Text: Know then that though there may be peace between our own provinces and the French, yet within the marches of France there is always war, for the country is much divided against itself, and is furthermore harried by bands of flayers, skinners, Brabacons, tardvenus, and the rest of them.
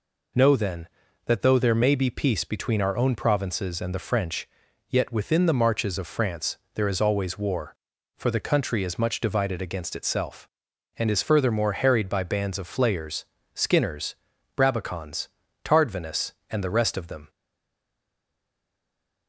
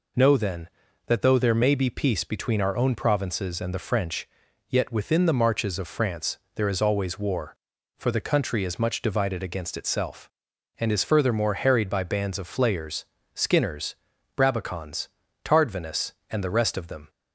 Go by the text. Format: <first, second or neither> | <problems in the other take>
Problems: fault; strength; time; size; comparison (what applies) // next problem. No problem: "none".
second | pauses between "France" and "there"; slight; at 6.5 s; 0.18 s long; slight in the second // stays silent after the last word; noticeable; from 17.2 s on; 2.0 s long